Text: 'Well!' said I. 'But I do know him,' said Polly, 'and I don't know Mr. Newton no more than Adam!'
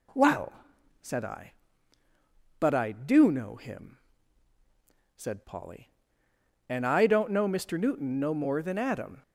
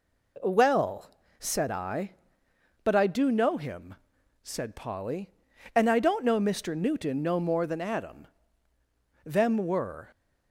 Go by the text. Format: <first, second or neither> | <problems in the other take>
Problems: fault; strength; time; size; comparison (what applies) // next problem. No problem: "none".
first | goes on to say "Them were"; noticeable; from 9.2 s on; 0.84 s long